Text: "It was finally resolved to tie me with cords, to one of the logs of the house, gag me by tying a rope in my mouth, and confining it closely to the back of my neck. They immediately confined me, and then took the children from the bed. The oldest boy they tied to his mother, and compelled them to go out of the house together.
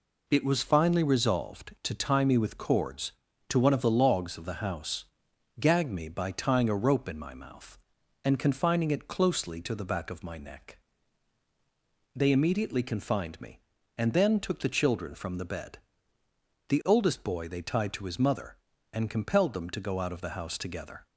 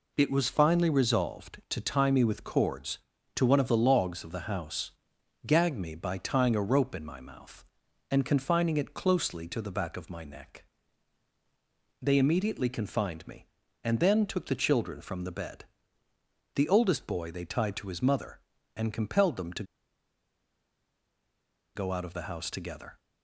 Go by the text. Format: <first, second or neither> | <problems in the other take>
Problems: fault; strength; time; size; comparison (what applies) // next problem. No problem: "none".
first | pauses between "to" and "go"; strong; at 19.6 s; 2.1 s long